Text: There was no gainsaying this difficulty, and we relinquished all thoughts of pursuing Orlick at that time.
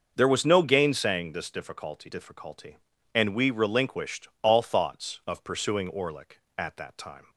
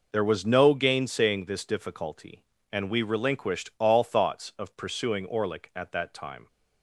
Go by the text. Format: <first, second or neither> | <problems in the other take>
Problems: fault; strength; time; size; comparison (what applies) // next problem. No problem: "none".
second | starts louder than the rest; until 1.1 s; 6 dB // says "difficulty" twice; at 2.0 s